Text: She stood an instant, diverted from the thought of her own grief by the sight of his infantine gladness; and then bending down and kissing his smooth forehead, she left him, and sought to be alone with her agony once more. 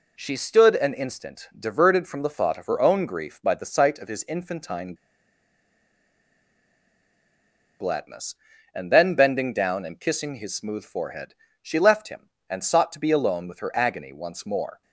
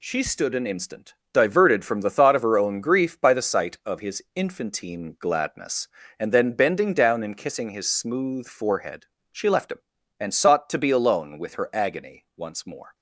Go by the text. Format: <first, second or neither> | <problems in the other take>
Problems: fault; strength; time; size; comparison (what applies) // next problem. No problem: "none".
second | pauses between "infantine" and "gladness"; strong; at 4.9 s; 2.8 s long